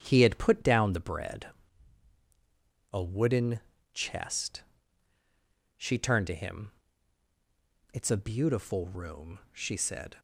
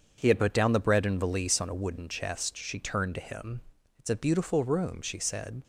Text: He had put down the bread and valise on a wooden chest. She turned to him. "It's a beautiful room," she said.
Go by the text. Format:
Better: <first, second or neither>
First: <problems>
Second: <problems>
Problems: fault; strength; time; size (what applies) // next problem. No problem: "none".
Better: second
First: starts louder than the rest; strong; until 1.0 s; 8.5 dB // skips "and valise on"; at 2.1 s // pauses between "wooden" and "chest"; slight; at 3.5 s; 0.34 s long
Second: starts louder than the rest; until 1.1 s; 7 dB